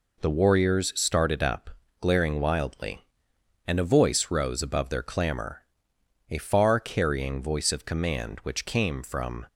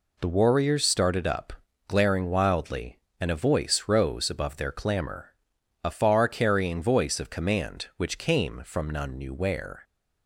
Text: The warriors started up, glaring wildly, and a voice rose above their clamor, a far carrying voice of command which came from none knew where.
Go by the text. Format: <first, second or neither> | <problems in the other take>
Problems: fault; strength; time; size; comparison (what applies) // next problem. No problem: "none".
second | stops before "none knew where"; at 9.4 s